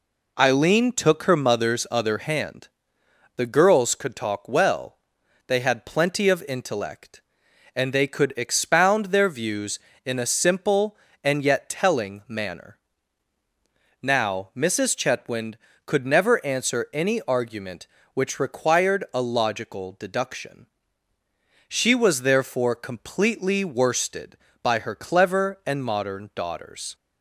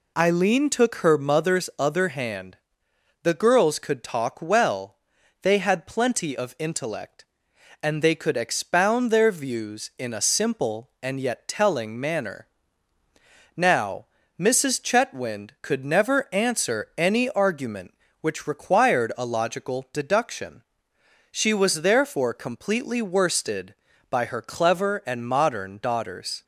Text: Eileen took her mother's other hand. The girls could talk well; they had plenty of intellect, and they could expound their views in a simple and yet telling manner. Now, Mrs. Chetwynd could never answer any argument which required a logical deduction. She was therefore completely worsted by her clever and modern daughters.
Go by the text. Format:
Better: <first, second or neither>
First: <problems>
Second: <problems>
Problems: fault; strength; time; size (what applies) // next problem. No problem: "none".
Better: neither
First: none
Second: none